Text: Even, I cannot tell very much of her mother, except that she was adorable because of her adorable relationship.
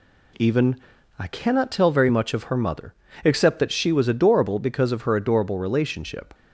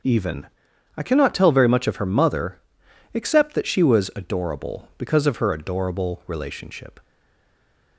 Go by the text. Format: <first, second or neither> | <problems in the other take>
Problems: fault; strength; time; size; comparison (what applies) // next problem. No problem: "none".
first | starts louder than the rest; until 1.5 s; 6.5 dB // stays silent after the last word; from 7.0 s on; 0.9 s long